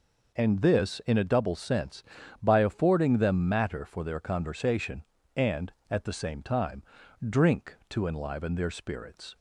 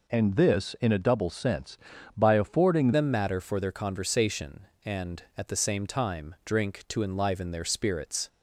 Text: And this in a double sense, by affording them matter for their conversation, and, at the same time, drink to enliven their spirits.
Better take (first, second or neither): first